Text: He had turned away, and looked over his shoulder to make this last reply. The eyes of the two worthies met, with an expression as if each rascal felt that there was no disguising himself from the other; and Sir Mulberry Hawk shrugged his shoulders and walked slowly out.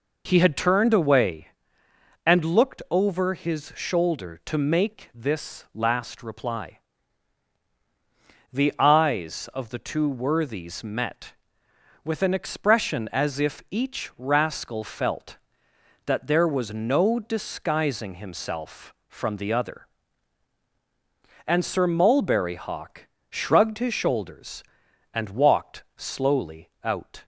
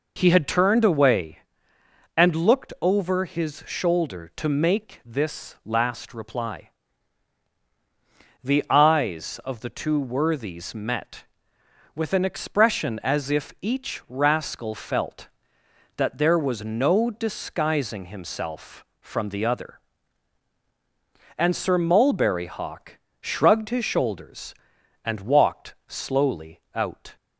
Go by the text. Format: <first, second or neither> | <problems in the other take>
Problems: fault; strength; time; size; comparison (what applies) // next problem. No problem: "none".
neither | pauses between "Hawk" and "shrugged"; slight; the same in both